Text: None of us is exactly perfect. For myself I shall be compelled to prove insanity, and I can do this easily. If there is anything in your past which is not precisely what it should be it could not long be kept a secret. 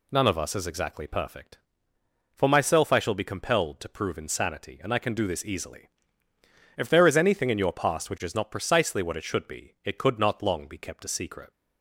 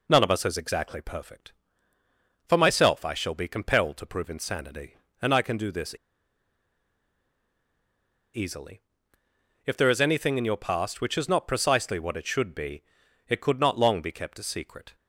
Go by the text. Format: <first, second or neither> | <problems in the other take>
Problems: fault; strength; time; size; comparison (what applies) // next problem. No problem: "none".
first | pauses between "this" and "easily"; strong; at 5.9 s; 2.4 s long // pauses between "be" and "it"; noticeable; at 12.8 s; 0.46 s long